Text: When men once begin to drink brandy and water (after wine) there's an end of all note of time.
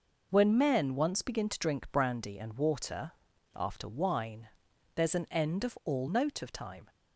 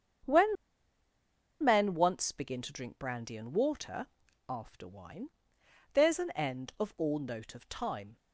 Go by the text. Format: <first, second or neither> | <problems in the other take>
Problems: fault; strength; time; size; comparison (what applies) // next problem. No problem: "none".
first | starts louder than the rest; strong; until 2.3 s; 7.5 dB // pauses between "When" and "men"; at 0.5 s; 1.0 s long